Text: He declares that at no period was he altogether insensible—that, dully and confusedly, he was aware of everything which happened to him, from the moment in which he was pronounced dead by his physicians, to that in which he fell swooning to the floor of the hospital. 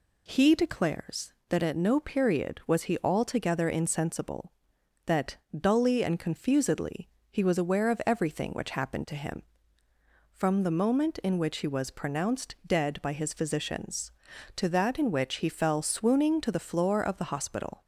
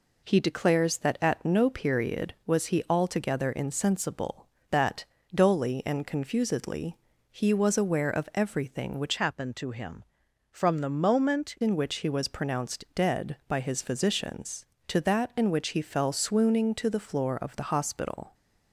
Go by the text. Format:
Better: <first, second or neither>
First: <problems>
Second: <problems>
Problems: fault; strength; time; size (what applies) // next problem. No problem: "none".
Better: first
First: none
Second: changes voice from "happened" to "moment"; from 9.1 to 11.5 s; 2.4 s long